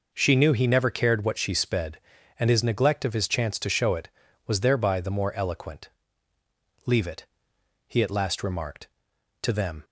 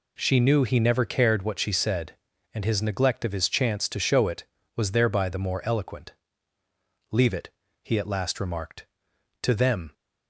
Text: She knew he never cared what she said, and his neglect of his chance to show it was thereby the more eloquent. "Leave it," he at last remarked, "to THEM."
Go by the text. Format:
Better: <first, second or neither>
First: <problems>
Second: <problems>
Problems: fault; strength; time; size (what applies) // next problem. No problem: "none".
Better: second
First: says "sped" for "said"; at 1.5 s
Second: none